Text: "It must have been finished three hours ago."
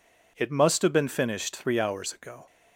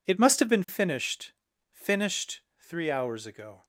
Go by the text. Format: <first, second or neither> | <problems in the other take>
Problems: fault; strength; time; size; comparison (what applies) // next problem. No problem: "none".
first | says "finished" twice; at 1.7 s